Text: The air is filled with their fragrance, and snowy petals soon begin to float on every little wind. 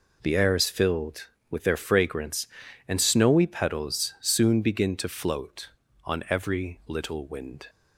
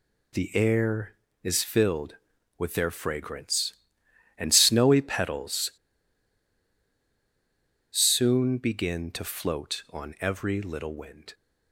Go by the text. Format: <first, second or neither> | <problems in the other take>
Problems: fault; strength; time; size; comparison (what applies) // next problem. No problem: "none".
first | pauses between "petals" and "soon"; strong; at 5.6 s; 2.2 s long